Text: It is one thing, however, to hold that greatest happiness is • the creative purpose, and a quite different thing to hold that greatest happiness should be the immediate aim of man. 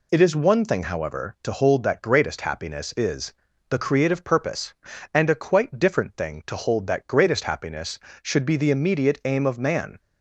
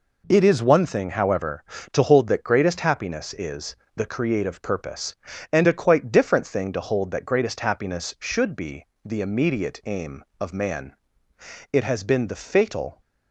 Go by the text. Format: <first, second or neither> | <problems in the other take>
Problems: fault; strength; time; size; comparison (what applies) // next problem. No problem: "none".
first | pauses between "be" and "the"; slight; at 8.8 s; 0.18 s long // goes on to say "It has been the fatal"; noticeable; from 11.7 s on; 1.2 s long